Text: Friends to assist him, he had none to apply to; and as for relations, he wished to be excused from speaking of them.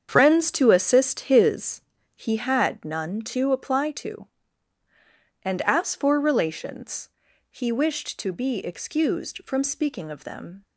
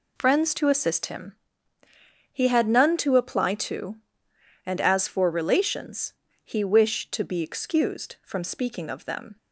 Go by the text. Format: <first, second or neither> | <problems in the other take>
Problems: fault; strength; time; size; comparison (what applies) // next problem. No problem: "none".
second | starts louder than the rest; strong; until 1.1 s; 8 dB // says "his" for "him"; at 1.2 s